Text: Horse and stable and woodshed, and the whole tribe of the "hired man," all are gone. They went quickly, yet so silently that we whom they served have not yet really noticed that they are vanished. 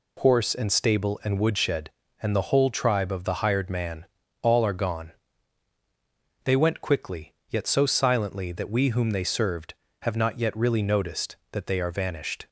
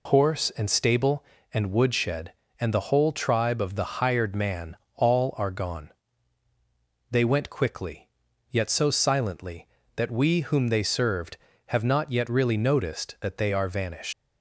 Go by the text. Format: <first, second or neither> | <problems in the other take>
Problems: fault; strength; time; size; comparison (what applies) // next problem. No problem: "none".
first | leaves "vanished" unfinished; at 14.1 s; 90 ms